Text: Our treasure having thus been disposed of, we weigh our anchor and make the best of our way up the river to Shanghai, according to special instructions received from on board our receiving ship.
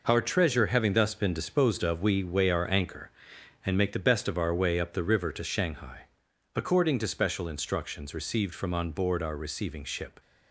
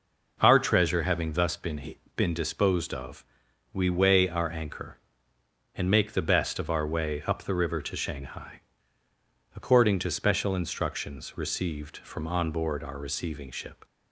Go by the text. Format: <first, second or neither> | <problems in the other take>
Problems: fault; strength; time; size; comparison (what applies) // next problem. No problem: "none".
first | says "been" twice; at 2.1 s